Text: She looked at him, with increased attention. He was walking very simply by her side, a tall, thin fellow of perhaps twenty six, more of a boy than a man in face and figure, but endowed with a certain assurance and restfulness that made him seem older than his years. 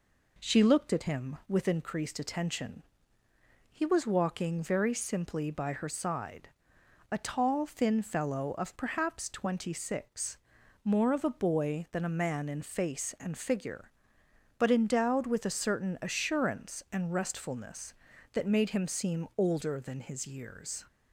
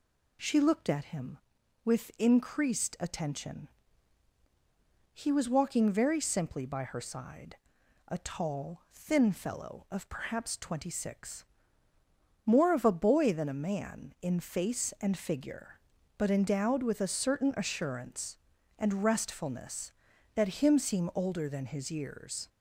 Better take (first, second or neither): first